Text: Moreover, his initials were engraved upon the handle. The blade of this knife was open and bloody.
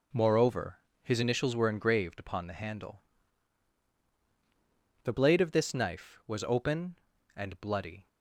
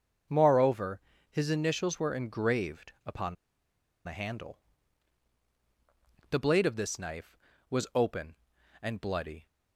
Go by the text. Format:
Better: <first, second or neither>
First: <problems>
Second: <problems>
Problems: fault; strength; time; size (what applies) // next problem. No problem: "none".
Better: first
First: none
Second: starts louder than the rest; until 1.6 s; 6 dB // pauses between "upon" and "the"; noticeable; at 3.3 s; 0.71 s long